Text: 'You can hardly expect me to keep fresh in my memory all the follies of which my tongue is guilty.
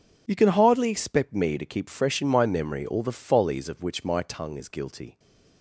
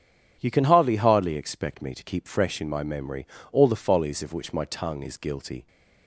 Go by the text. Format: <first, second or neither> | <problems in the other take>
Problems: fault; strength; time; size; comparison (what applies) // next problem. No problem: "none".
first | says "hardly" twice; at 0.9 s // pauses between "memory" and "all"; slight; at 3.2 s; 0.26 s long